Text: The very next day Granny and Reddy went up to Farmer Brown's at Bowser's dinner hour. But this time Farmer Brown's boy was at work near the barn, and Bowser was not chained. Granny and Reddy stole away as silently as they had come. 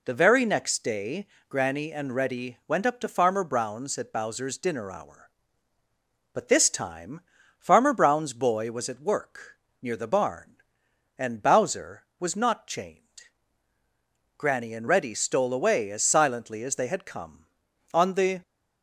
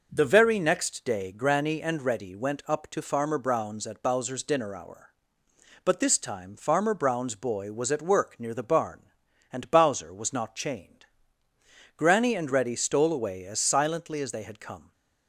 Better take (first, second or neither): second